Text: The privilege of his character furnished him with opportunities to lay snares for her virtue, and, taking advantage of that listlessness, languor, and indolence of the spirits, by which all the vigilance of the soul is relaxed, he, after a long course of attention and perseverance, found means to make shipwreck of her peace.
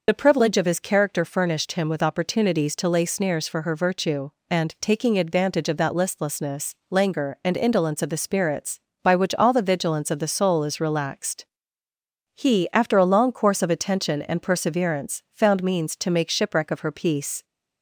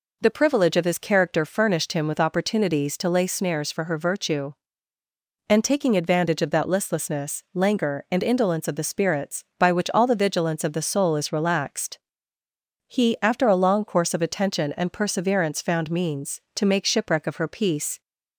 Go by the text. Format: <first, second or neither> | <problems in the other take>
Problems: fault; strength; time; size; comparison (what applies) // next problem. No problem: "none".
second | loses the start of "The"; at 0.0 s; 35 ms